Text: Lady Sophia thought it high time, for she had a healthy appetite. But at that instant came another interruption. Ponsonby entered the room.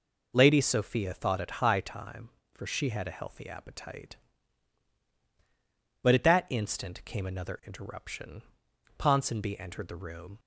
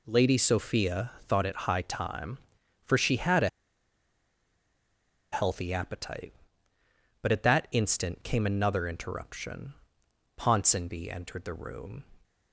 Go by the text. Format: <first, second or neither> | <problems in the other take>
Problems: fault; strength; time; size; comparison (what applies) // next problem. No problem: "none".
first | pauses between "a" and "healthy"; strong; at 3.4 s; 1.8 s long